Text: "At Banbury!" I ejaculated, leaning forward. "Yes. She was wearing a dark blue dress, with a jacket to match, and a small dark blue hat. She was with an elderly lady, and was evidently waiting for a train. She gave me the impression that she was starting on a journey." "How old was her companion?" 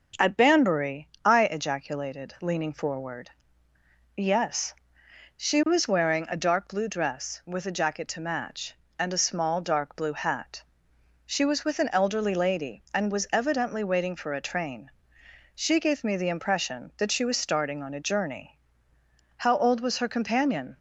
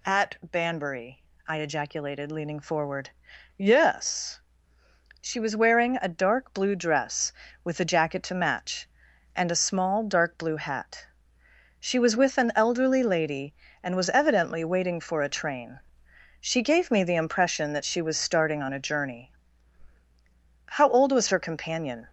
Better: neither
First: none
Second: none

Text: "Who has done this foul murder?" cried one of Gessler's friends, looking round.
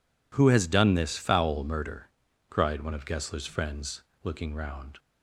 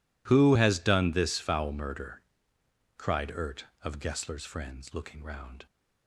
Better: first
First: none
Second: says "ert" for "one"; at 3.2 s

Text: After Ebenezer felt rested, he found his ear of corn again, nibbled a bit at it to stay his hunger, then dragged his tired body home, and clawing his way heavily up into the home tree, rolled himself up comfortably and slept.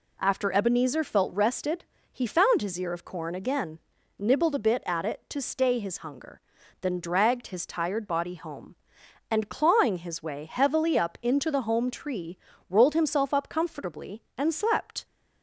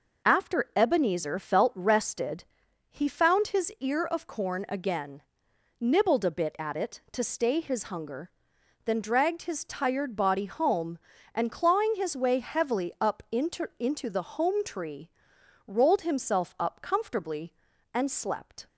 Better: first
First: none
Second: says "into" twice; at 13.7 s

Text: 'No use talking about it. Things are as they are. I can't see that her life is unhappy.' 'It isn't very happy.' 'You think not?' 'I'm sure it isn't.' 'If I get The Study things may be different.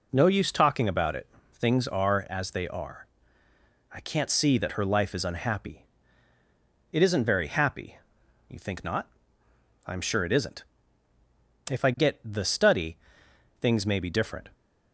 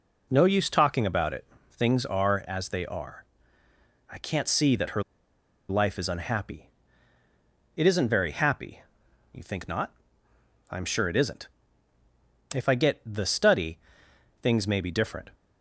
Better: first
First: pauses between "Study" and "things"; noticeable; at 12.9 s; 0.62 s long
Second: pauses between "her" and "life"; noticeable; at 5.0 s; 0.66 s long // pauses between "Study" and "things"; noticeable; at 13.7 s; 0.62 s long

